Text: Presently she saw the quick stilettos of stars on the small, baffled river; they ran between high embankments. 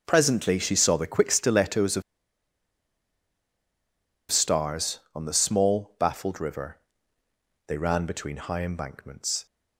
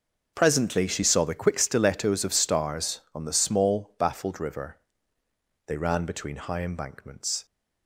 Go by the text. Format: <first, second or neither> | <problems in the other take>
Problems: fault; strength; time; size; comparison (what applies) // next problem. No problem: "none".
second | starts louder than the rest; noticeable; until 1.0 s; 6 dB; noticeable in the second // pauses between "of" and "stars"; strong; at 2.0 s; 2.2 s long